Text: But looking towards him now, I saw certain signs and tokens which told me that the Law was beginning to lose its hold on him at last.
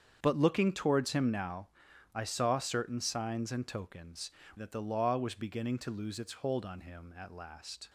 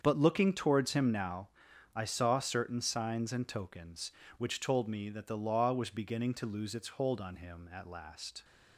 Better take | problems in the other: second | starts louder than the rest; strong; until 1.2 s; 7.5 dB; strong in the second // skips "which told me"; at 4.4 s

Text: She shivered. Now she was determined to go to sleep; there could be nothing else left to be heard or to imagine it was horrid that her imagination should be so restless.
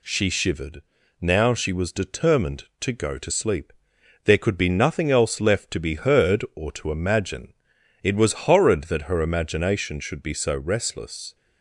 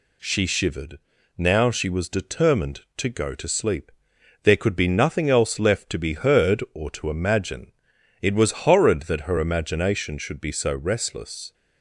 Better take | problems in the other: neither | pauses between "imagine" and "it"; noticeable; the same in both

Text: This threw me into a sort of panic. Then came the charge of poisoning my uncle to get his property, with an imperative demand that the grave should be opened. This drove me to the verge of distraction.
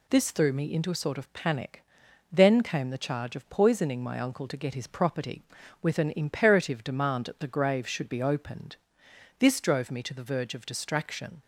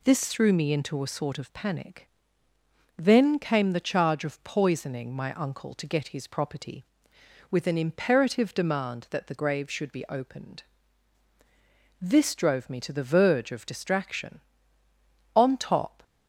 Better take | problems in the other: first | goes on to say "On top"; noticeable; from 15.3 s on; 0.68 s long

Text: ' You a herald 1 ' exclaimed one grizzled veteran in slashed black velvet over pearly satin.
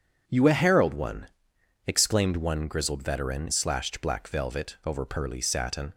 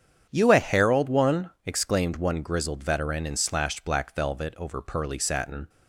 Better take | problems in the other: second | starts louder than the rest; until 1.2 s; 7 dB; strong in the second // skips "in"; at 3.4 s

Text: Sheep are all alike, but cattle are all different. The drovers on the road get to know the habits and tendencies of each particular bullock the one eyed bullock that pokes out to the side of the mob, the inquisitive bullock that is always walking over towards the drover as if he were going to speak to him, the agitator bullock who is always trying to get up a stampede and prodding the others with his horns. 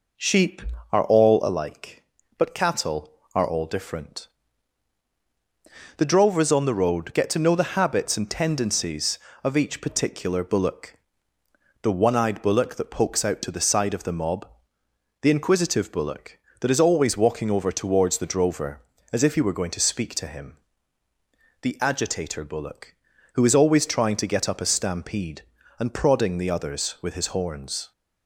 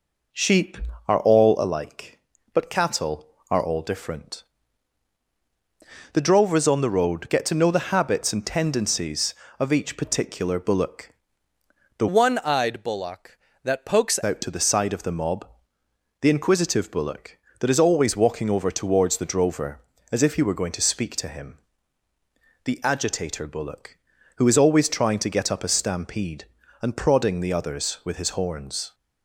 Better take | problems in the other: first | pauses between "bullock" and "the"; noticeable; at 11.0 s; 0.88 s long; noticeable in the first // changes voice from "one" to "pokes"; from 12.0 to 14.1 s; 2.1 s long

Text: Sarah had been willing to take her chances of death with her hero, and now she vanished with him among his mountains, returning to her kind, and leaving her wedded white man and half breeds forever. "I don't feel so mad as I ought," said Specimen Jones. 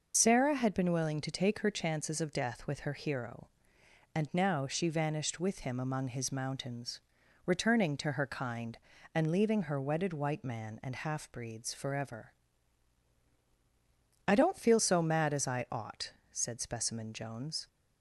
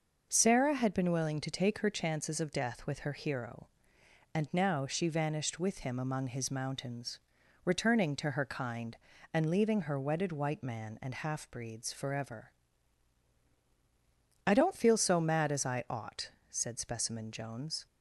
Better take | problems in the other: second | loses the start of "Sarah"; at 0.1 s; 45 ms // starts louder than the rest; noticeable; until 1.1 s; 6 dB; noticeable in the second

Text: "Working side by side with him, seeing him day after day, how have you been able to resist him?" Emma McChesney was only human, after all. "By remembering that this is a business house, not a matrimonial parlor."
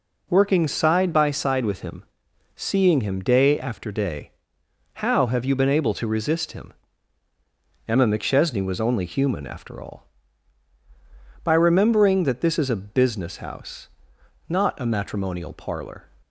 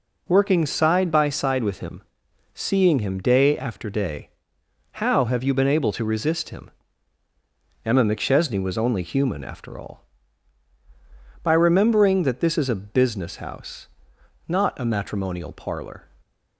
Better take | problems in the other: neither | none

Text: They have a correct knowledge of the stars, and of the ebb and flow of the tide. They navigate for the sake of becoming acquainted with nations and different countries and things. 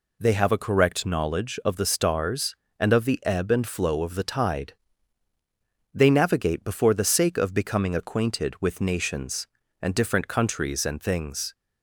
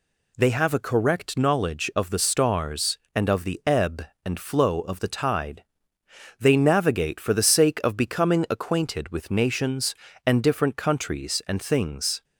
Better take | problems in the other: second | says "before" for "for"; at 6.6 s

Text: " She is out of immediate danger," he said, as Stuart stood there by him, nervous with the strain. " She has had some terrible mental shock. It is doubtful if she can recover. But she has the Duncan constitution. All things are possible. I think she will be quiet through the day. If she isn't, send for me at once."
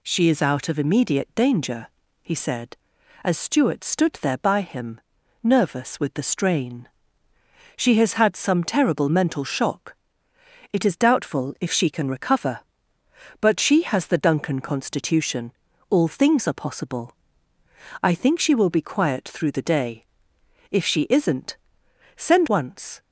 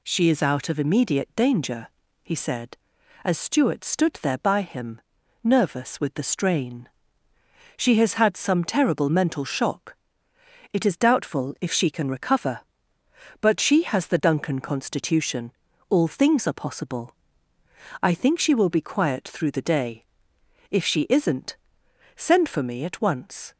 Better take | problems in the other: second | skips "for me at"; at 22.4 s

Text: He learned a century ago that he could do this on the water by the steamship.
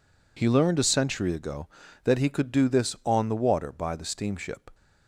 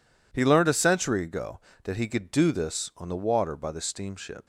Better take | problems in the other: neither | none

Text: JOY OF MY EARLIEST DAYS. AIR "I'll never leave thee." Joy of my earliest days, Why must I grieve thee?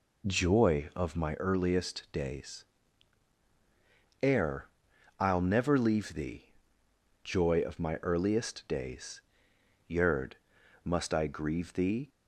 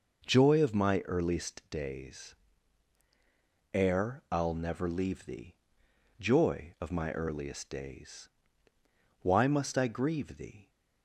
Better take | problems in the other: second | pauses between "AIR" and "I'll"; noticeable; at 4.6 s; 0.54 s long // says "Yerd" for "Why"; at 9.8 s

